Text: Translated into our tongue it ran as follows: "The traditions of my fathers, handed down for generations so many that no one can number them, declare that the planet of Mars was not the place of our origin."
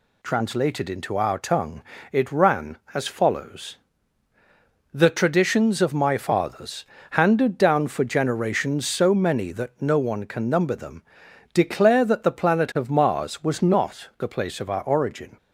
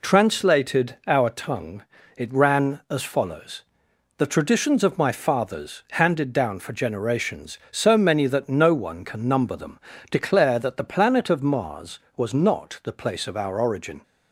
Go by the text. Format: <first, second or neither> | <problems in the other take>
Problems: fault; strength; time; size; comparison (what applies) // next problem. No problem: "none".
first | skips "into"; at 1.0 s // pauses between "tongue" and "it"; slight; at 1.8 s; 0.34 s long; slight in the first